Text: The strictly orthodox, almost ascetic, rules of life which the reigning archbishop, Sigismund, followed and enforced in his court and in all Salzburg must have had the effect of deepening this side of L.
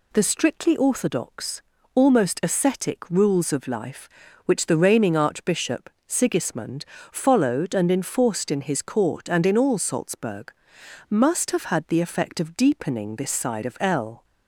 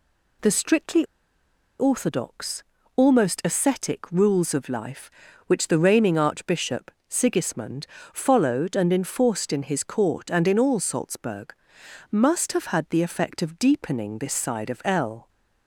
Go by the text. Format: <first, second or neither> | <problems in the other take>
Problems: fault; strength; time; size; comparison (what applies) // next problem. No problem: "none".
first | pauses between "strictly" and "orthodox"; noticeable; at 1.0 s; 0.76 s long // pauses between "Salzburg" and "must"; noticeable; at 11.5 s; 0.58 s long; noticeable in the first